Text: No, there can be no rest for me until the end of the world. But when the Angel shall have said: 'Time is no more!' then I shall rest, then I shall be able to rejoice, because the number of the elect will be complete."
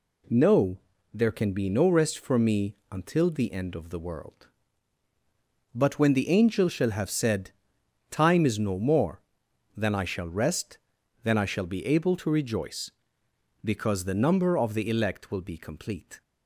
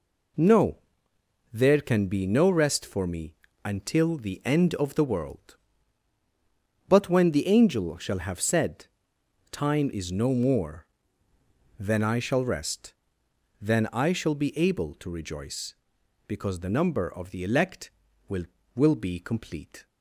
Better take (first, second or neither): first